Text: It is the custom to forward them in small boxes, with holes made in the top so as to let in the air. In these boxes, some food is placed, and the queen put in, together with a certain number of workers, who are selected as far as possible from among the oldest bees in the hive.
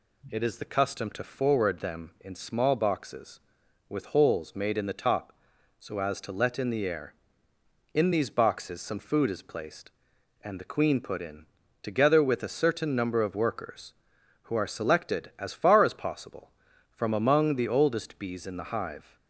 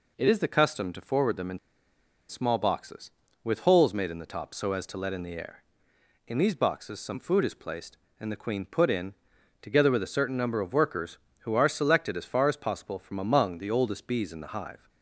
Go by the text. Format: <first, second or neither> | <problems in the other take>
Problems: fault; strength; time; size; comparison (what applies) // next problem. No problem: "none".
first | pauses between "in" and "small"; noticeable; at 1.5 s; 0.70 s long